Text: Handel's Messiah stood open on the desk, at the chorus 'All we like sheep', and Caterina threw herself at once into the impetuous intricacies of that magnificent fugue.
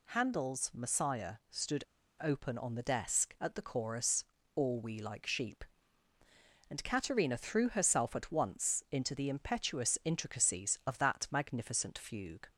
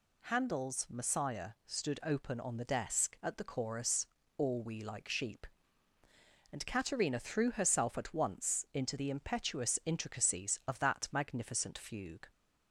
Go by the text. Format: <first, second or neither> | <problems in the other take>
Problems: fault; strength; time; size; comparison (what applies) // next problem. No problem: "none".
second | pauses between "stood" and "open"; slight; at 1.8 s; 0.35 s long // pauses between "chorus" and "All"; slight; at 4.2 s; 0.30 s long; slight in the second